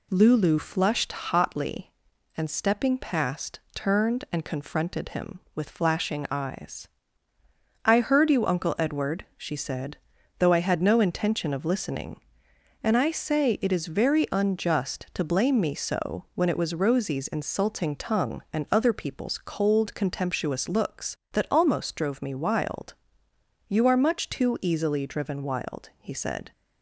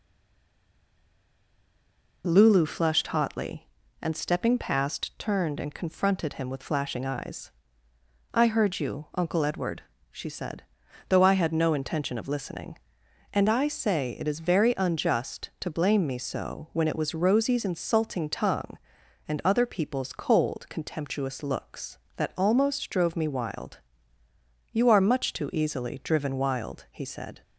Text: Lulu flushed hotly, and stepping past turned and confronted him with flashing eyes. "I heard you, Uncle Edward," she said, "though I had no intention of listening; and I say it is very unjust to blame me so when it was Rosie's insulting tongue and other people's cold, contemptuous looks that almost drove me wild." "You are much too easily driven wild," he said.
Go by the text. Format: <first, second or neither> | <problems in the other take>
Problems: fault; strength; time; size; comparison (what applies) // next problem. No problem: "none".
first | stays silent before the first word; until 2.2 s; 2.2 s long